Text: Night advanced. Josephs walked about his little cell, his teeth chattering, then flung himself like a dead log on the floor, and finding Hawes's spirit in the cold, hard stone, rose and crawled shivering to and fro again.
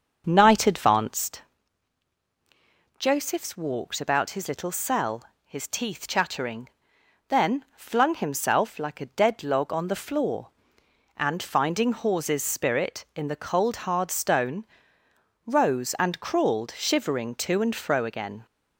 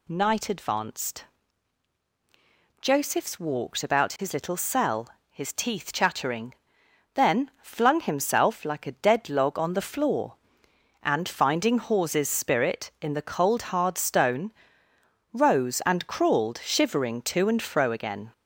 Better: second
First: starts louder than the rest; until 1.3 s; 6.5 dB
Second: none

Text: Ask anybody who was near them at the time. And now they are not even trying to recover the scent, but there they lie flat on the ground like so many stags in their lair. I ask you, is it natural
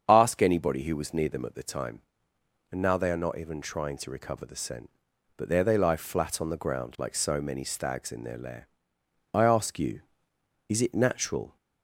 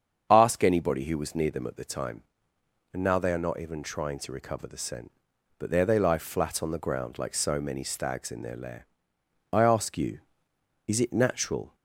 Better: neither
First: starts louder than the rest; strong; until 1.0 s; 7.5 dB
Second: starts louder than the rest; strong; until 1.3 s; 7.5 dB

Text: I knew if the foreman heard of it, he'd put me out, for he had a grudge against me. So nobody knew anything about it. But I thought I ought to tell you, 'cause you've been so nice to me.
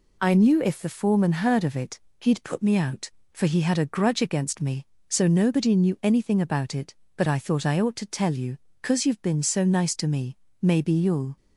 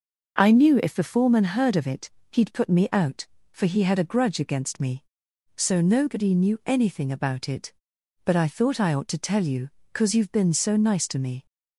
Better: second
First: goes on to say "Maybe you'll"; noticeable; from 10.6 s on; 0.74 s long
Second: none

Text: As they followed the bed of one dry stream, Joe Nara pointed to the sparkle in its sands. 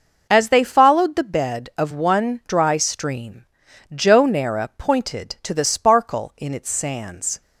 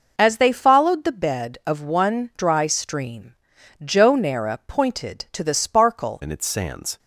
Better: first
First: none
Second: changes voice at "in"; from 6.2 s on; 0.7 s long

